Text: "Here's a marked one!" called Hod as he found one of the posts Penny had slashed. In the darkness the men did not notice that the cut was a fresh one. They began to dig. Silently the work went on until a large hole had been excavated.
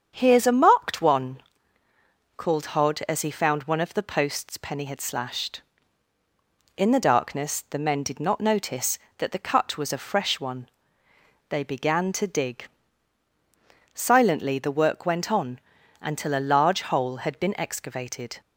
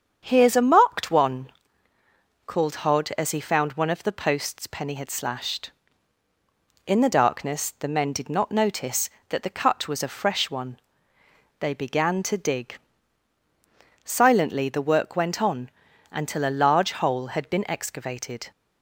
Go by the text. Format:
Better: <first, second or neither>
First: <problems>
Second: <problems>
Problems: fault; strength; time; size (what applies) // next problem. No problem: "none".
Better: neither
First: starts louder than the rest; strong; until 1.1 s; 7.5 dB // pauses between "on" and "until"; at 15.5 s; 0.40 s long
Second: starts louder than the rest; strong; until 1.2 s; 7.5 dB // pauses between "on" and "until"; at 15.6 s; 0.40 s long